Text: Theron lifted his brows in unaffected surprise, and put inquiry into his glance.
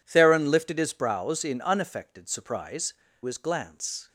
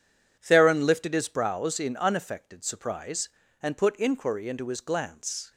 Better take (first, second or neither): second